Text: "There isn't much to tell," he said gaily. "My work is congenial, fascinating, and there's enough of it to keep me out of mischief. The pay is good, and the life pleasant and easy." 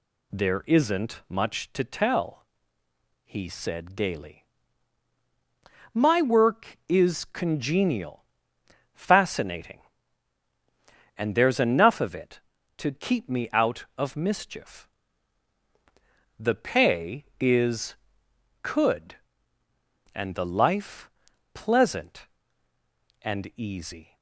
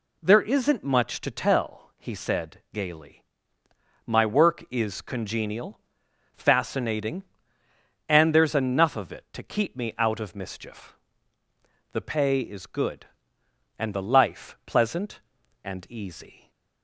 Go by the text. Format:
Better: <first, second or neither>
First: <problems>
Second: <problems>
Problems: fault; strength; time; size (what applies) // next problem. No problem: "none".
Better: second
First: says "could" for "good"; at 18.6 s // pauses between "life" and "pleasant"; at 21.1 s; 0.44 s long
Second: none